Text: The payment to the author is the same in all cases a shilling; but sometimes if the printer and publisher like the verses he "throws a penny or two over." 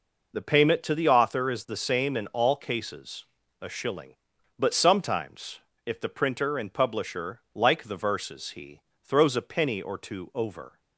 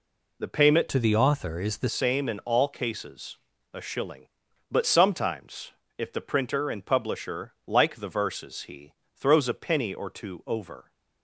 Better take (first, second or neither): first